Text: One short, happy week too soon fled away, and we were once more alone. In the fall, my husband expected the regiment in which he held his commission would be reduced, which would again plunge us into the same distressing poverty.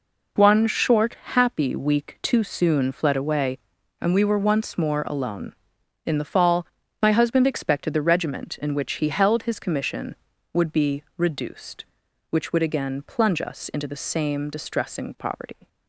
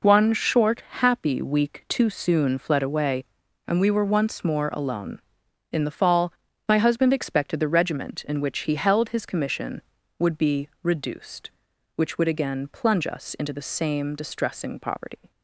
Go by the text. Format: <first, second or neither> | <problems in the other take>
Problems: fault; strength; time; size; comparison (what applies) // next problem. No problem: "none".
neither | none